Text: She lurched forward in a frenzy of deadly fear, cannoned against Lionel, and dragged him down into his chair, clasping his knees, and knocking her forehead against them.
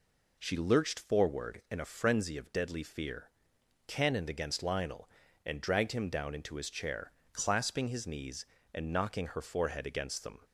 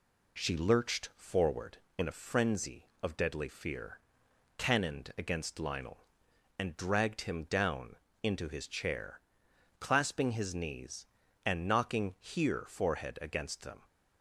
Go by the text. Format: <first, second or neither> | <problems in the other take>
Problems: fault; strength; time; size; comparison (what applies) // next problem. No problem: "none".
first | pauses between "down" and "into"; slight; at 7.9 s; 0.28 s long // says "here" for "her"; at 12.1 s